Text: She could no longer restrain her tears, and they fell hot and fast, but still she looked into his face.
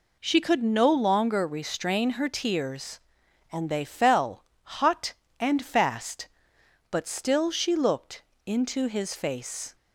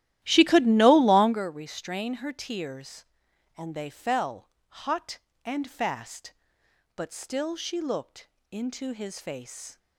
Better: first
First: pauses between "fell" and "hot"; slight; at 4.4 s; 0.20 s long // pauses between "looked" and "into"; slight; at 8.2 s; 0.24 s long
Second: starts louder than the rest; strong; until 1.4 s; 13.5 dB // pauses between "fell" and "hot"; slight; at 4.4 s; 0.20 s long // pauses between "looked" and "into"; slight; at 8.2 s; 0.24 s long

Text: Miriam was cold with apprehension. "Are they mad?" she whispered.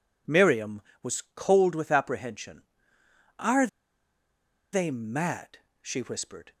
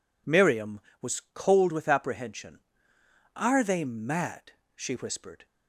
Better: second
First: pauses between "Are" and "they"; at 3.6 s; 1.0 s long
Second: none

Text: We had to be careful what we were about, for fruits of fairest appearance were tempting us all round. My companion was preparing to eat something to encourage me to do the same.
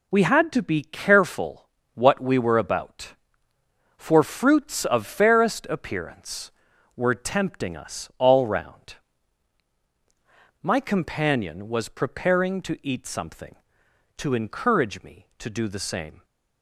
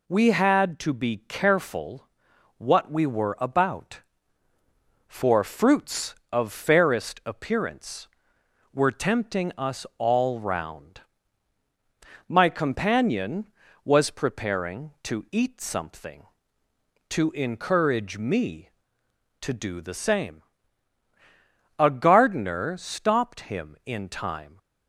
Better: first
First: pauses between "careful" and "what"; slight; at 1.6 s; 0.26 s long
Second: pauses between "careful" and "what"; noticeable; at 2.0 s; 0.50 s long // goes on to say "A gardener stopped him in time"; strong; from 21.7 s on; 2.8 s long

